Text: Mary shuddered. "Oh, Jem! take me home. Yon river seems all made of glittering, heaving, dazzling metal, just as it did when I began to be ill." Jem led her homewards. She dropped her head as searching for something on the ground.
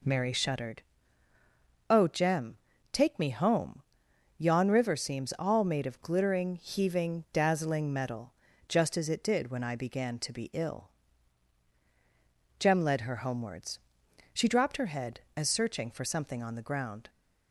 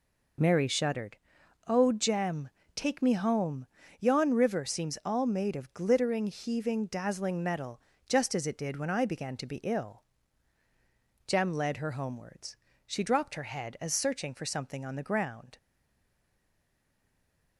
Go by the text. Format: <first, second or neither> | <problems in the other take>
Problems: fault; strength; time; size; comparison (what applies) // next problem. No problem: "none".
first | stays silent after the last word; noticeable; from 15.5 s on; 2.0 s long